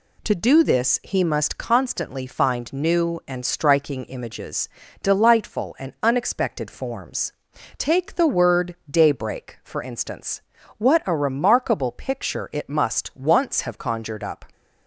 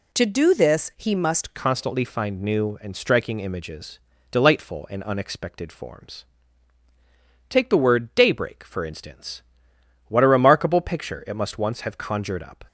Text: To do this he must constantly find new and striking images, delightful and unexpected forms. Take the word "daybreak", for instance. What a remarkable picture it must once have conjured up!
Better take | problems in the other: first | changes voice at "constantly"; from 1.5 s on; 11.1 s long

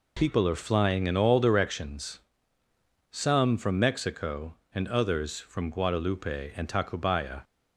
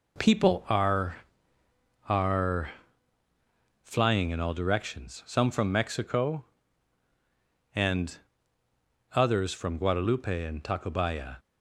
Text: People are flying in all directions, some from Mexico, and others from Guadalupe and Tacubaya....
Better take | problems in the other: first | says "are" twice; at 2.0 s // pauses between "and" and "others"; noticeable; at 8.1 s; 0.98 s long

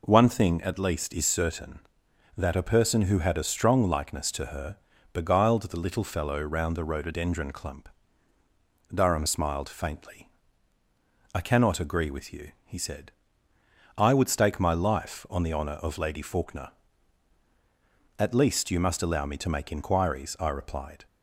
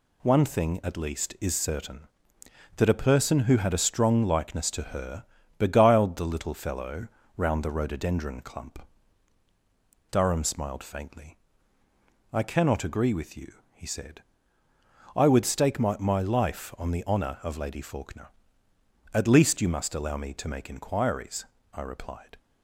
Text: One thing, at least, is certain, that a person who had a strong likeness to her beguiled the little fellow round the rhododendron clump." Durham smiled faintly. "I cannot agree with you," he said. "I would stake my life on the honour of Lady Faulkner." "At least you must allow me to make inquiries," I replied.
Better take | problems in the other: first | pauses between "her" and "beguiled"; slight; at 5.2 s; 0.34 s long; also in the first // pauses between "fellow" and "round"; slight; at 7.0 s; 0.30 s long // says "my" twice; at 15.9 s

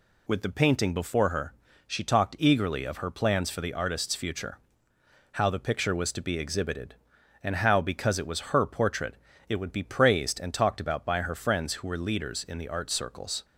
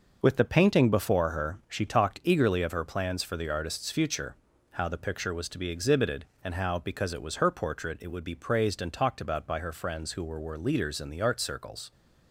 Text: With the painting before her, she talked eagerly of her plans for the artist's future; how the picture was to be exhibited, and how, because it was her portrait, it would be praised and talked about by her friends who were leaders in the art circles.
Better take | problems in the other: first | says "were" twice; at 10.3 s

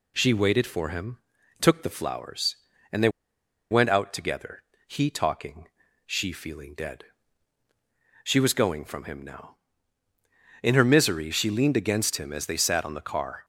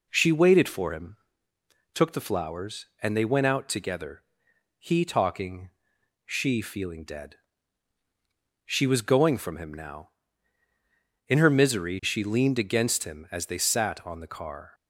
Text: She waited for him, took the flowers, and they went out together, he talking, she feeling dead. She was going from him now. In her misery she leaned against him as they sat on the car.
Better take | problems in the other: second | pauses between "they" and "went"; noticeable; at 3.0 s; 0.61 s long

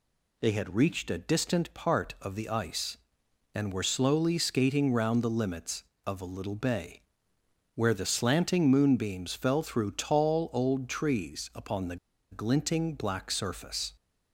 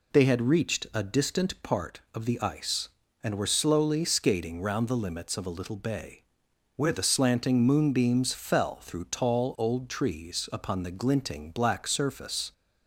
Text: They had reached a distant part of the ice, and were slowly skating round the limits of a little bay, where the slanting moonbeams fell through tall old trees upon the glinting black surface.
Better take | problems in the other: second | pauses between "the" and "glinting"; slight; at 11.9 s; 0.35 s long

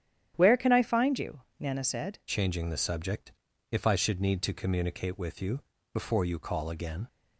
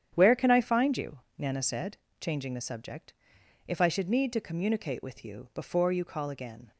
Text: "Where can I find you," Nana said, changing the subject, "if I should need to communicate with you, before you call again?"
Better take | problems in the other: second | starts louder than the rest; strong; until 1.3 s; 10 dB; strong in the second // changes voice at "changing"; from 2.2 s on; 4.8 s long

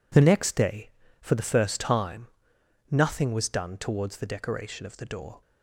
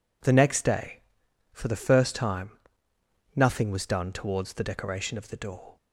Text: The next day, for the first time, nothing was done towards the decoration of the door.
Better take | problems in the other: neither | none

